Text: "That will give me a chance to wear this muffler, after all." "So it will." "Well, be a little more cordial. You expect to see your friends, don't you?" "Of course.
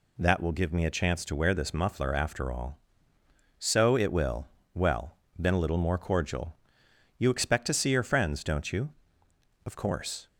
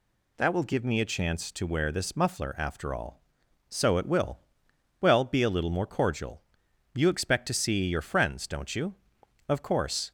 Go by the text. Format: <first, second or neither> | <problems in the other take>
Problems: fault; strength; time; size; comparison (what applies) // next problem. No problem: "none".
second | says "been" for "be"; at 5.3 s